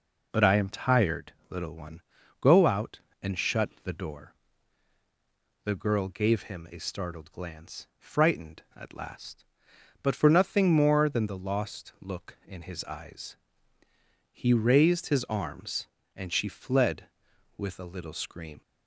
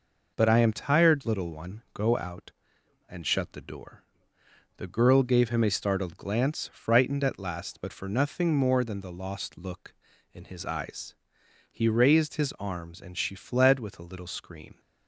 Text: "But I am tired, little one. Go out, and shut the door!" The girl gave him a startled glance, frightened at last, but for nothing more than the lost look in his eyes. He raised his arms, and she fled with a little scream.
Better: neither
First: none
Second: none

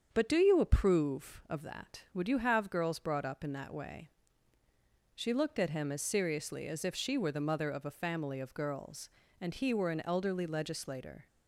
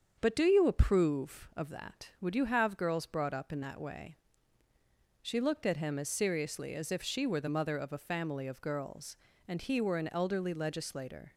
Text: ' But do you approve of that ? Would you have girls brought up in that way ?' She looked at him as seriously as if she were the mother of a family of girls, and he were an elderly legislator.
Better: neither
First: starts louder than the rest; strong; until 1.1 s; 7.5 dB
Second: starts louder than the rest; strong; until 1.1 s; 7.5 dB

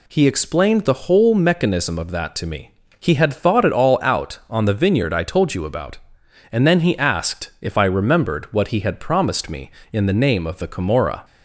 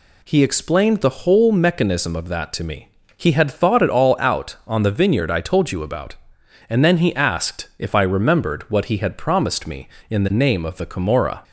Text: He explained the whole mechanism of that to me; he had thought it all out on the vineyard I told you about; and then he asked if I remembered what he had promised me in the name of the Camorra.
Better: neither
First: none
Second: none

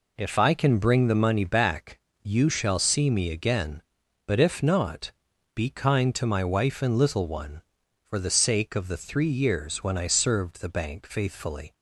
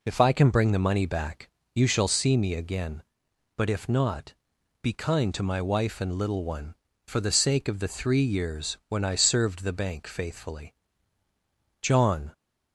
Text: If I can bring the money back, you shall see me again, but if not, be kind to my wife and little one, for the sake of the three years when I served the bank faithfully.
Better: first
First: none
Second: goes on to say "JOHN"; from 11.8 s on; 0.50 s long

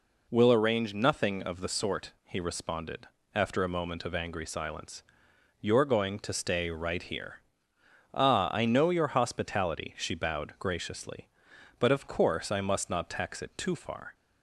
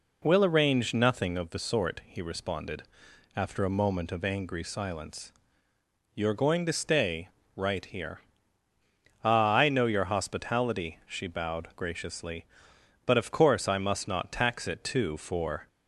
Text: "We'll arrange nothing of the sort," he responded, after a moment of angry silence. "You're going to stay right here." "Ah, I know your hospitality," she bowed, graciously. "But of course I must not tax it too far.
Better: first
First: none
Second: pauses between "stay" and "right"; slight; at 7.2 s; 0.26 s long // says "for" for "far"; at 15.1 s

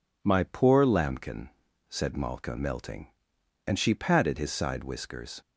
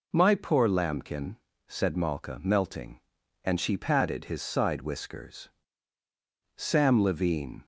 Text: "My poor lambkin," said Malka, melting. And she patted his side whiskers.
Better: first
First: none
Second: goes on to say "Sam Levine"; noticeable; from 6.5 s on; 1.1 s long

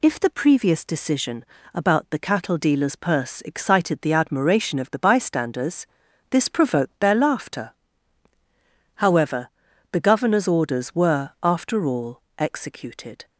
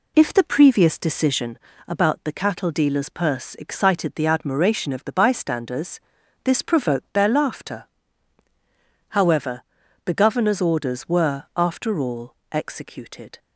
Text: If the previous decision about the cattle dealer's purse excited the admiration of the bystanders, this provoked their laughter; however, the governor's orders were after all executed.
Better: first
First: pauses between "decision" and "about"; slight; at 1.4 s; 0.30 s long // pauses between "all" and "executed"; slight; at 12.2 s; 0.16 s long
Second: starts louder than the rest; slight; until 1.5 s; 2.5 dB // pauses between "decision" and "about"; slight; at 1.5 s; 0.30 s long // pauses between "all" and "executed"; slight; at 12.3 s; 0.16 s long

